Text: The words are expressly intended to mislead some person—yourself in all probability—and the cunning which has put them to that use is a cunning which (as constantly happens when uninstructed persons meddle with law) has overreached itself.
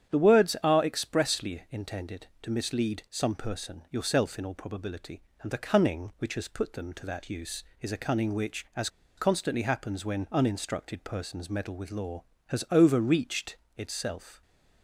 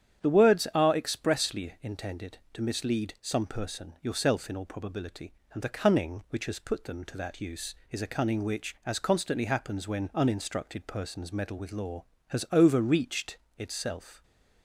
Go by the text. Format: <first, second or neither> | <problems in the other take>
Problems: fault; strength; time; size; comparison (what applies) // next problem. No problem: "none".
second | starts louder than the rest; strong; until 1.1 s; 9 dB; strong in the second // pauses between "as" and "constantly"; slight; at 8.8 s; 0.28 s long // pauses between "overreached" and "itself"; slight; at 13.5 s; 0.22 s long; slight in the second